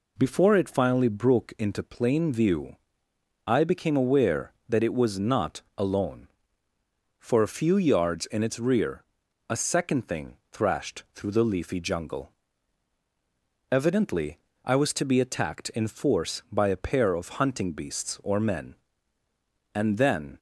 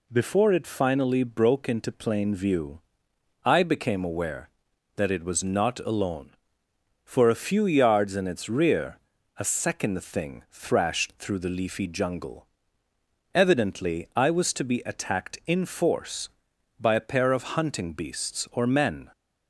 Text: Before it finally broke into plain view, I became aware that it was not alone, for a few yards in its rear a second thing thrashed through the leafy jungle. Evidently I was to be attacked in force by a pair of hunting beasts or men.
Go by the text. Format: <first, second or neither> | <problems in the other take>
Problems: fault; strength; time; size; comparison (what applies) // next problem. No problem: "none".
second | pauses between "rear" and "a"; noticeable; at 9.0 s; 0.46 s long; also in the second // pauses between "Evidently" and "I"; slight; at 14.3 s; 0.26 s long // goes on to say "And then"; noticeable; from 19.7 s on; 0.64 s long